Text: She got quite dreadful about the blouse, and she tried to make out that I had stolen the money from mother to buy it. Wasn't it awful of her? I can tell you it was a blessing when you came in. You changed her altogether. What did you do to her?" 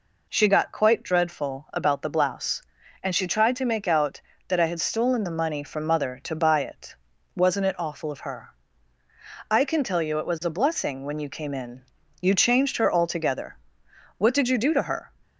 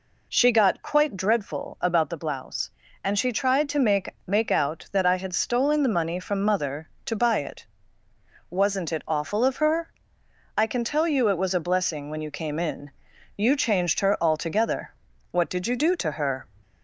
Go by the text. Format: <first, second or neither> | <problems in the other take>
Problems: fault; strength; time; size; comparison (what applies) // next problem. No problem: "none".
first | says "make" twice; at 4.2 s